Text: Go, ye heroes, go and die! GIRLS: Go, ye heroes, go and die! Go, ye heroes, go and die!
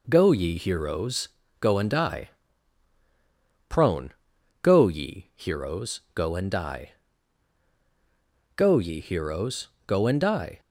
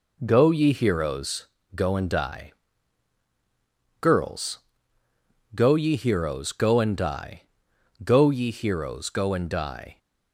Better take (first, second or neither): second